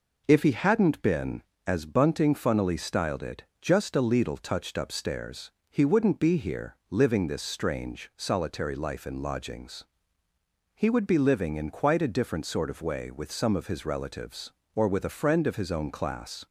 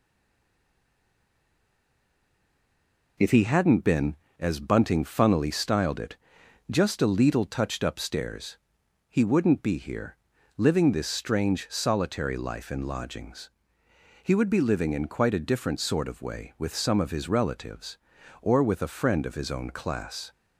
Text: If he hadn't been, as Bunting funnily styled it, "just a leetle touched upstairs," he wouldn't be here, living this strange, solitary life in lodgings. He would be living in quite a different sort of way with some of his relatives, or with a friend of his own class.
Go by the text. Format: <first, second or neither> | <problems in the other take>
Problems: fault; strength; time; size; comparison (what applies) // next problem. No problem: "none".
first | stays silent before the first word; strong; until 3.1 s; 3.1 s long